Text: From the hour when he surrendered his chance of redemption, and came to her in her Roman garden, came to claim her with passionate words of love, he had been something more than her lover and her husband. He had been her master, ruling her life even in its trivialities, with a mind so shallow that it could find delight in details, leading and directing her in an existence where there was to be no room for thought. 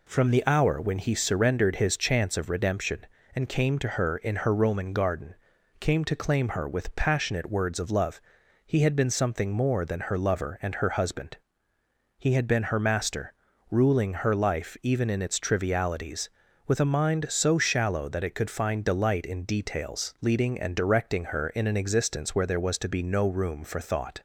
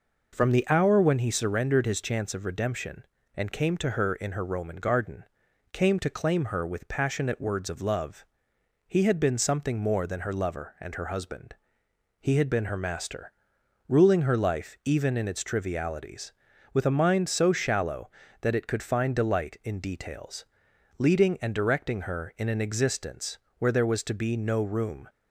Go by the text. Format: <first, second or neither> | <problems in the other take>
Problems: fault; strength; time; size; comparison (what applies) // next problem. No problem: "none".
first | pauses between "existence" and "where"; slight; at 23.3 s; 0.22 s long // stops before "for thought"; at 25.0 s